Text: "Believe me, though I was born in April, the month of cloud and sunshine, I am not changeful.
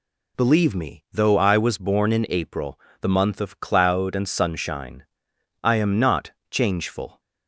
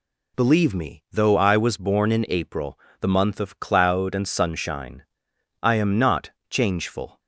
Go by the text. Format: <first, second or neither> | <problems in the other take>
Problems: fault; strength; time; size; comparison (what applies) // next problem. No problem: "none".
neither | pauses between "not" and "changeful"; slight; the same in both